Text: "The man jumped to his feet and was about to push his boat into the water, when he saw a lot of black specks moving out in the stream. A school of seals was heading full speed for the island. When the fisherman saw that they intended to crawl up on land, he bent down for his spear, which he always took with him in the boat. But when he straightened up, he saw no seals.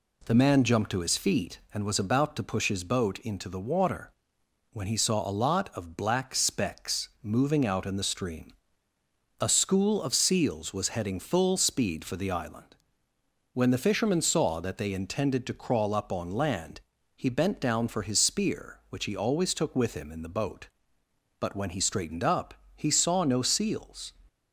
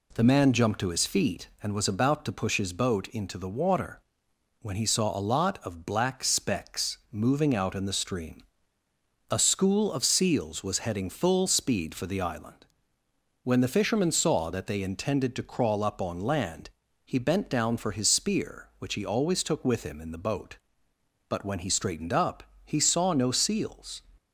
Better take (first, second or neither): neither